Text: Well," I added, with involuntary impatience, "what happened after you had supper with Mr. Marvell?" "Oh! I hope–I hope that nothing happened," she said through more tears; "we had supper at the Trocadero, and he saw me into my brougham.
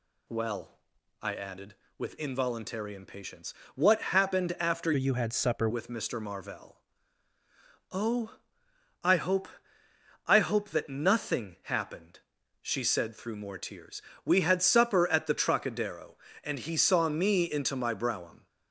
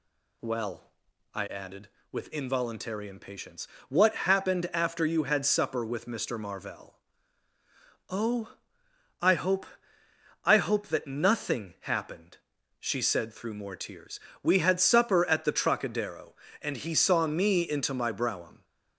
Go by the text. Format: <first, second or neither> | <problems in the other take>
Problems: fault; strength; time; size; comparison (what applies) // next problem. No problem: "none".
second | changes voice from "you" to "supper"; from 4.9 to 5.6 s; 0.7 s long